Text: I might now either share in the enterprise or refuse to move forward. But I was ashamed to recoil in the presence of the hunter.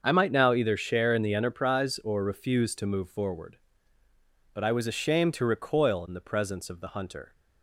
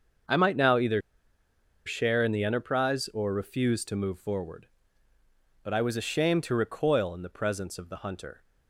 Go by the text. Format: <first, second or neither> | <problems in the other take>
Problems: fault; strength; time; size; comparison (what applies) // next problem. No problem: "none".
first | starts louder than the rest; until 2.1 s; 6.5 dB; also in the first // pauses between "either" and "share"; noticeable; at 1.0 s; 0.85 s long